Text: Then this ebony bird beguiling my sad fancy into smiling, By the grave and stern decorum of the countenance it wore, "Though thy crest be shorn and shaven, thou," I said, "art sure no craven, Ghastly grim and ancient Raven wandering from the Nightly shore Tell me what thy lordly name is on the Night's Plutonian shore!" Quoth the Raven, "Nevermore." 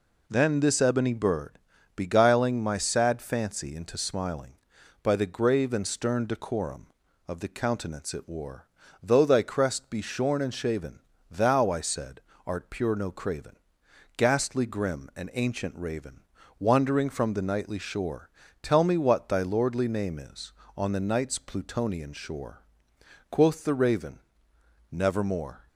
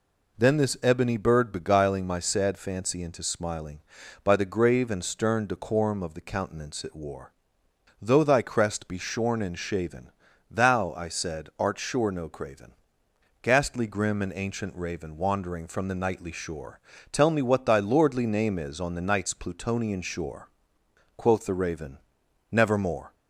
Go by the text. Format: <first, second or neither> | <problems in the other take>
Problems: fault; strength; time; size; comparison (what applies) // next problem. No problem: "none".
second | pauses between "bird" and "beguiling"; slight; at 1.5 s; 0.36 s long // says "pure" for "sure"; at 12.7 s // pauses between "Raven" and "wandering"; slight; at 16.2 s; 0.34 s long // pauses between "shore" and "Tell"; slight; at 18.2 s; 0.34 s long; slight in the second